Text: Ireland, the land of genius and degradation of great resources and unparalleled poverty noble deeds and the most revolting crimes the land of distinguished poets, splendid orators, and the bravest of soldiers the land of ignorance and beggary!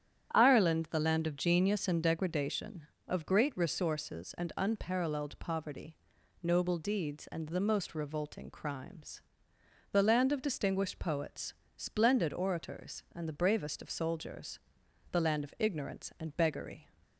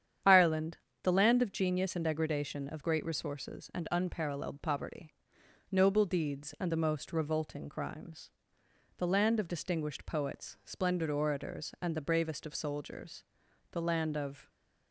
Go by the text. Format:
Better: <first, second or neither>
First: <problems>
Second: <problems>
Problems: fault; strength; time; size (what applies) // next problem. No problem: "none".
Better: first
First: starts louder than the rest; strong; until 1.3 s; 9.5 dB // pauses between "poverty" and "noble"; noticeable; at 5.9 s; 0.46 s long // pauses between "crimes" and "the"; noticeable; at 9.1 s; 0.72 s long // pauses between "soldiers" and "the"; noticeable; at 14.5 s; 0.50 s long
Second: starts louder than the rest; strong; until 1.5 s; 9 dB // pauses between "poverty" and "noble"; noticeable; at 5.1 s; 0.58 s long // pauses between "crimes" and "the"; noticeable; at 8.2 s; 0.66 s long // pauses between "soldiers" and "the"; noticeable; at 13.2 s; 0.48 s long // stops before "ignorance and beggary"; at 14.4 s